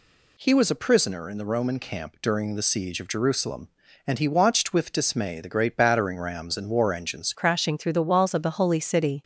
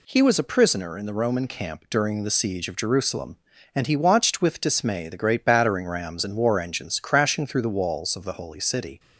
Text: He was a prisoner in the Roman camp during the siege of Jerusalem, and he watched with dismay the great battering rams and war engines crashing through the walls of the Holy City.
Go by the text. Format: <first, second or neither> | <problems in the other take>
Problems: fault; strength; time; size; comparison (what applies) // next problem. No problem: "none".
second | changes voice at "crashing"; from 7.3 s on; 1.9 s long